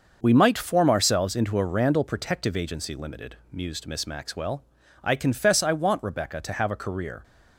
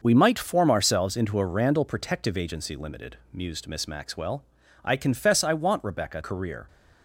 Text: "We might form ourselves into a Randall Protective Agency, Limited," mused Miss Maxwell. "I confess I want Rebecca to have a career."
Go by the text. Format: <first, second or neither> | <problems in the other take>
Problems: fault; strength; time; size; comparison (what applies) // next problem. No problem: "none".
first | starts louder than the rest; noticeable; until 1.0 s; 6 dB; also in the first // skips "to have a"; at 6.2 s